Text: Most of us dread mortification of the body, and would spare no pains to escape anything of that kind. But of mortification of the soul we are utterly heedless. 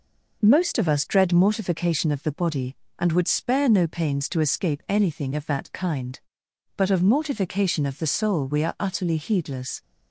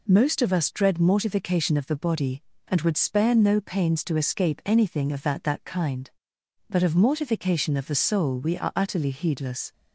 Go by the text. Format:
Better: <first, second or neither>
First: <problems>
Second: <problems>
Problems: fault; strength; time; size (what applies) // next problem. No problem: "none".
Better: first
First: none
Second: says "that" twice; at 5.4 s